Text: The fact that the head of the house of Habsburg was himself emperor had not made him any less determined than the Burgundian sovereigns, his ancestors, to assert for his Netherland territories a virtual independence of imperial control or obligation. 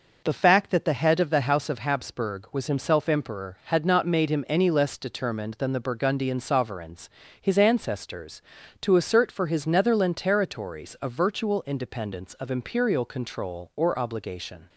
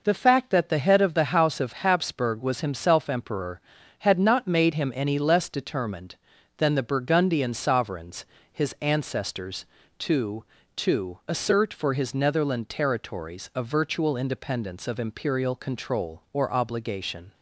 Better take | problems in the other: first | says "to" twice; at 10.7 s

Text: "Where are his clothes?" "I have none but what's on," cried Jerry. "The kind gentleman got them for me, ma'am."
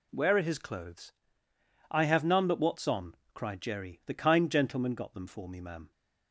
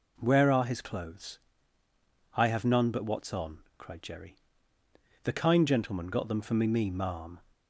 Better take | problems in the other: first | says "me" twice; at 6.6 s

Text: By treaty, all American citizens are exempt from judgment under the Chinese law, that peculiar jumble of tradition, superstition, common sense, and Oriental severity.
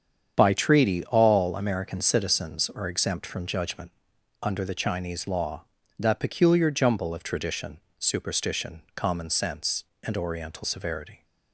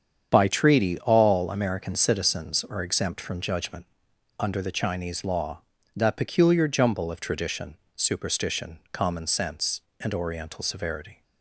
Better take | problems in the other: neither | starts louder than the rest; strong; the same in both // pauses between "judgment" and "under"; noticeable; the same in both

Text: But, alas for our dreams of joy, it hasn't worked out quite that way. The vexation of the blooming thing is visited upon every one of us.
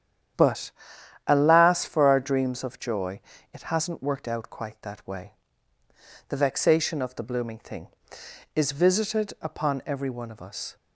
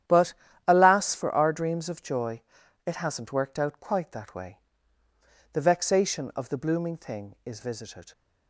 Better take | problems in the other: first | starts louder than the rest; strong; until 1.4 s; 10.5 dB; strong in the first // stops before "upon every one of us"; at 8.1 s

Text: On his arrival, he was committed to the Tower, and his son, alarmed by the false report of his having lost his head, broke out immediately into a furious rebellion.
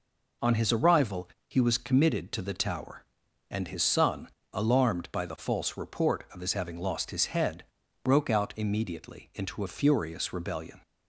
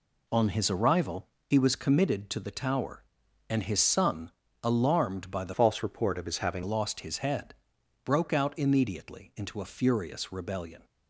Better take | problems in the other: first | changes voice from "false" to "having"; from 5.5 to 6.6 s; 1.1 s long

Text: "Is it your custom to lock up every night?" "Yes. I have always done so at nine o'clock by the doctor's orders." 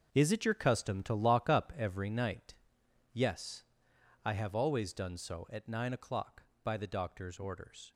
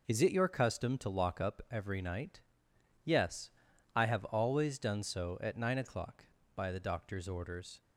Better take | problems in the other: second | gets quieter; strong; throughout; 10.5 dB

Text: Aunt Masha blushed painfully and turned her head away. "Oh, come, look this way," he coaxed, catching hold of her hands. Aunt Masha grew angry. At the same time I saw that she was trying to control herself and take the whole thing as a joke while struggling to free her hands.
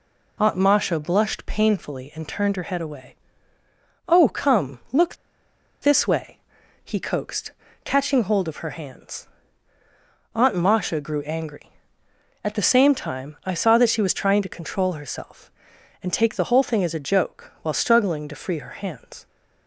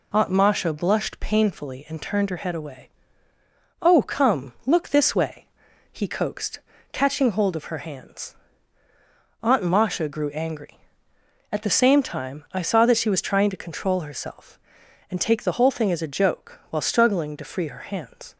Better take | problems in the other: second | pauses between "look" and "this"; noticeable; at 5.1 s; 0.66 s long

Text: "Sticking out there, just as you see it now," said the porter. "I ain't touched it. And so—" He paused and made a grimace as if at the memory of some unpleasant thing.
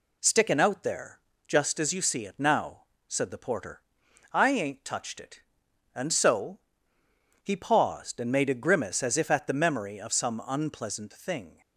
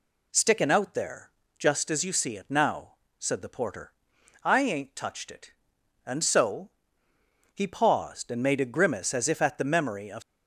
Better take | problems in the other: first | stops before "some unpleasant thing"; at 10.2 s

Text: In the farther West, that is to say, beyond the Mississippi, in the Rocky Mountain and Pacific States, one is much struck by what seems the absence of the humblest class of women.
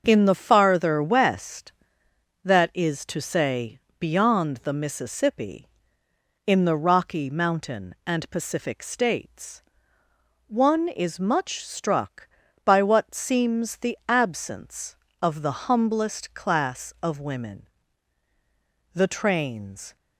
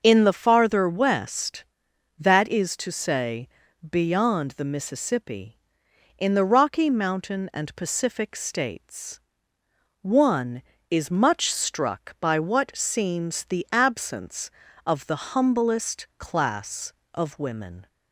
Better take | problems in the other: second | starts louder than the rest; until 1.0 s; 6.5 dB; also in the second // goes on to say "The trains"; noticeable; from 18.9 s on; 1.0 s long

